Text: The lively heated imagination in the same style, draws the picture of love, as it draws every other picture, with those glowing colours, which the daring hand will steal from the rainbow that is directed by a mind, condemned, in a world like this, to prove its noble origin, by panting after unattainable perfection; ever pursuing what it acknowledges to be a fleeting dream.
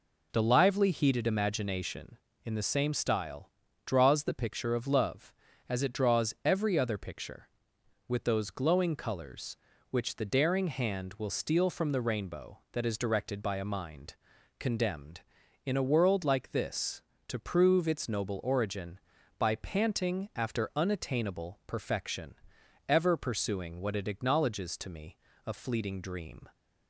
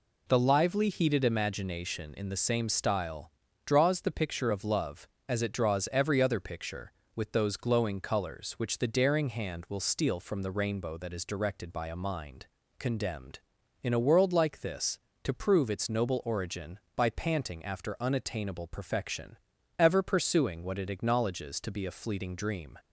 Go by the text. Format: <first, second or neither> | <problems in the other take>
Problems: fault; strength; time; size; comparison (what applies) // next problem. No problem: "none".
second | says "me" for "be"; at 24.9 s